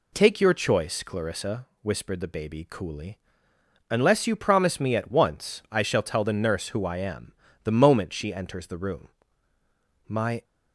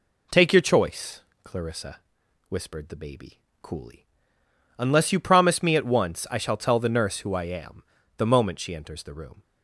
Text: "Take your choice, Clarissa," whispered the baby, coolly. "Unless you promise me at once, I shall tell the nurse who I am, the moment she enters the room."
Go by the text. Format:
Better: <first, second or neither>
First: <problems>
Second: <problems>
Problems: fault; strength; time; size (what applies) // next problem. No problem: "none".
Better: second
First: goes on to say "My"; slight; from 10.0 s on; 0.36 s long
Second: none